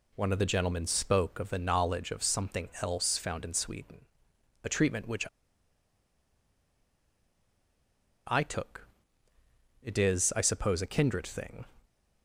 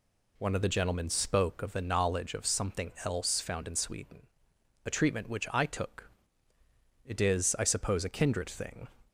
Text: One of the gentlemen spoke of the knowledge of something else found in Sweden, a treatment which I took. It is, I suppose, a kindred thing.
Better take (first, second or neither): second